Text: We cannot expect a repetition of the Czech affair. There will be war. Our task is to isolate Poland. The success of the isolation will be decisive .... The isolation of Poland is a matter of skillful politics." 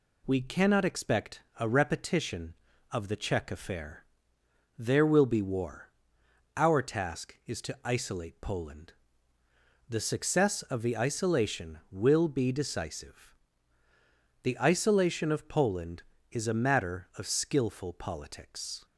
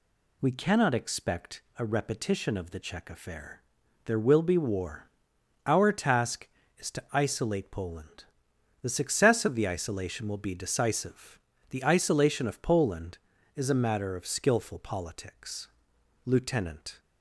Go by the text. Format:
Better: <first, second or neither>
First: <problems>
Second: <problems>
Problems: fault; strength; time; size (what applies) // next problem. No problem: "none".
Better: first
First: pauses between "expect" and "a"; slight; at 1.4 s; 0.18 s long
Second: pauses between "expect" and "a"; slight; at 1.6 s; 0.16 s long // goes on to say "Lieutenant"; noticeable; from 16.2 s on; 0.74 s long